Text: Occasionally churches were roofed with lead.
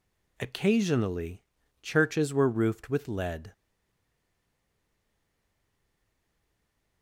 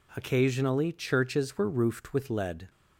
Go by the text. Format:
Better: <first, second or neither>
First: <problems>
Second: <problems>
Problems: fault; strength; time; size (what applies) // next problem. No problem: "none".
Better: second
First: pauses between "Occasionally" and "churches"; at 1.4 s; 0.40 s long // stays silent after the last word; strong; from 3.5 s on; 3.5 s long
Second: none